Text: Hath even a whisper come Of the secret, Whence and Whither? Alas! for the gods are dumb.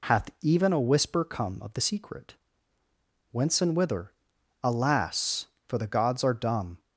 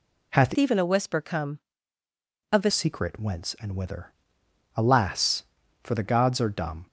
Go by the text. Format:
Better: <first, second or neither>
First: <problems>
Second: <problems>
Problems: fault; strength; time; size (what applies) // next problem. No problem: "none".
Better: first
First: none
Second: changes voice from "even" to "the"; from 0.5 to 2.7 s; 2.2 s long